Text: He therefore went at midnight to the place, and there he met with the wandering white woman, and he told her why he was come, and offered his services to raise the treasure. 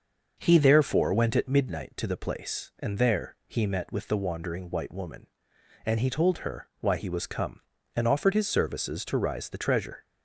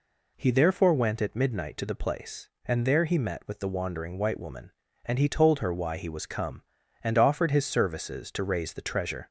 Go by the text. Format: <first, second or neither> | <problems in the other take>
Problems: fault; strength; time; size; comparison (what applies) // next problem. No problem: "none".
second | starts louder than the rest; until 1.3 s; 6.5 dB // says "rise" for "raise"; at 9.1 s